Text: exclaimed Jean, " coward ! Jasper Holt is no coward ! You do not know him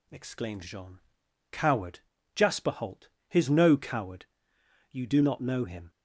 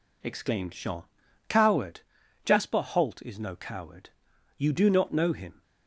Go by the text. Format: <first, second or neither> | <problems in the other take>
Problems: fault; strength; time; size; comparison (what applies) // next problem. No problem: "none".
second | says "his" for "is"; at 3.2 s